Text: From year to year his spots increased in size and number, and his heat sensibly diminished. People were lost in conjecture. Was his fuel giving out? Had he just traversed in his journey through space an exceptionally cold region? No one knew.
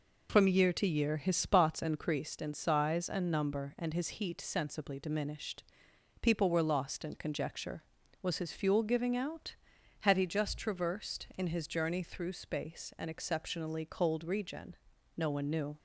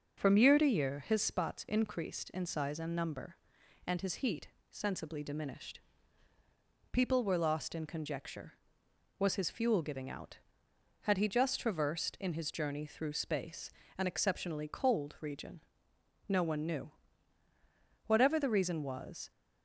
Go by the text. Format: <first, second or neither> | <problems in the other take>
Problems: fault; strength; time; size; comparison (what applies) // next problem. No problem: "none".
first | starts louder than the rest; until 1.2 s; 6 dB // pauses between "heat" and "sensibly"; slight; at 4.4 s; 0.20 s long // pauses between "space" and "an"; slight; at 13.7 s; 0.26 s long // goes on to say "Whatever the reason was"; noticeable; from 18.0 s on; 1.2 s long